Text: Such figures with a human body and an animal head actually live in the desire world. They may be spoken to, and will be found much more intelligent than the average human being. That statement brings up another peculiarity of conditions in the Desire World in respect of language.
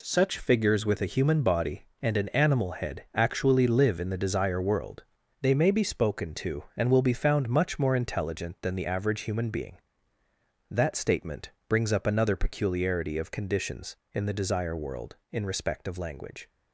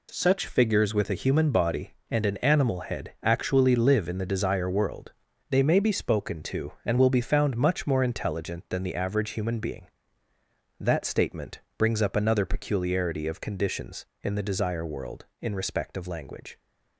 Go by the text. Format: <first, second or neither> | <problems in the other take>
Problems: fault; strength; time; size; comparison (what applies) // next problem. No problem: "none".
neither | pauses between "statement" and "brings"; slight; the same in both